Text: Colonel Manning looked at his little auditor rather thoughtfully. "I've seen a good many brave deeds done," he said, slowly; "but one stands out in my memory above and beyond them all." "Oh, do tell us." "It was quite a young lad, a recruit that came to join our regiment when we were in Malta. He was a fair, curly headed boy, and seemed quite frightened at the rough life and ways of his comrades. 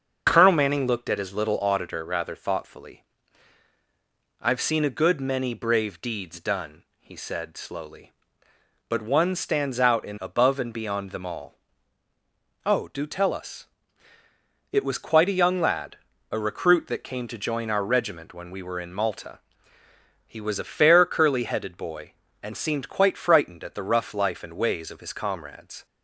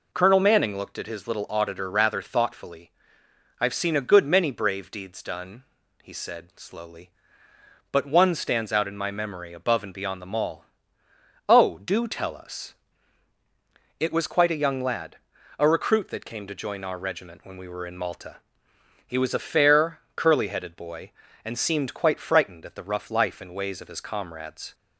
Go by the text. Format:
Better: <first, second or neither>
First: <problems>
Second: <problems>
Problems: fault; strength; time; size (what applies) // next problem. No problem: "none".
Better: second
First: starts louder than the rest; until 1.2 s; 6 dB // skips "my memory"; at 10.1 s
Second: none